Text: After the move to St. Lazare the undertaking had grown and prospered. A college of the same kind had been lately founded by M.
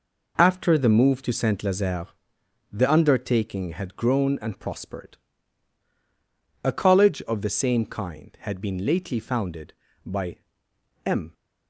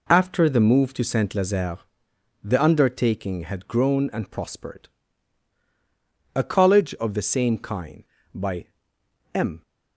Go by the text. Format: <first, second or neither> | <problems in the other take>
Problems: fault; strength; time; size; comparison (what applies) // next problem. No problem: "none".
first | pauses between "Lazare" and "the"; noticeable; at 1.7 s; 0.64 s long; noticeable in the first // skips "had been lately founded"; at 8.1 s // pauses between "by" and "M"; noticeable; at 8.6 s; 0.68 s long; noticeable in the first